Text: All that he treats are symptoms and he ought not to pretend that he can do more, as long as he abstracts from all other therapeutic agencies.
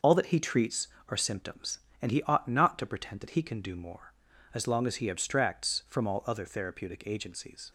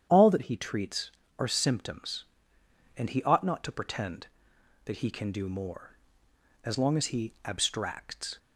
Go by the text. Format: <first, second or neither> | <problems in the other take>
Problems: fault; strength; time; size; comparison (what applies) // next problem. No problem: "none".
first | starts louder than the rest; strong; until 1.1 s; 9 dB; noticeable in the first // stops before "from all other therapeutic agencies"; at 8.3 s